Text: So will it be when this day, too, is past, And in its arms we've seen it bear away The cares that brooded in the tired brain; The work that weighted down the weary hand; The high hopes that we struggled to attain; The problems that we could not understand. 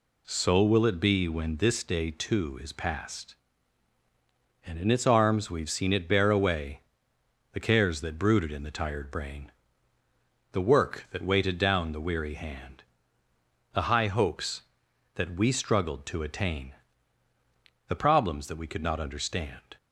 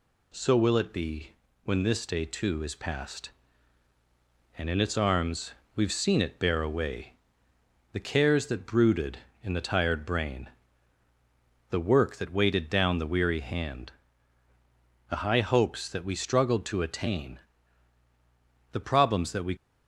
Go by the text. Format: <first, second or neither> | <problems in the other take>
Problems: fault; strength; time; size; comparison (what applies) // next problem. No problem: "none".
first | pauses between "be" and "when"; slight; at 1.3 s; 0.32 s long // pauses between "arms" and "we've"; slight; at 5.5 s; 0.22 s long // pauses between "away" and "The"; noticeable; at 7.1 s; 0.80 s long; noticeable in the first // stops before "could not understand"; at 19.5 s